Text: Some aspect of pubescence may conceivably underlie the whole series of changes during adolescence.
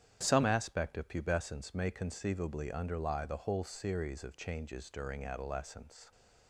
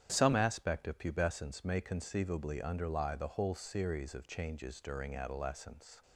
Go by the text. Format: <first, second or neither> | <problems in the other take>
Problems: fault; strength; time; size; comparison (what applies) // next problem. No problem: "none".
neither | starts louder than the rest; strong; the same in both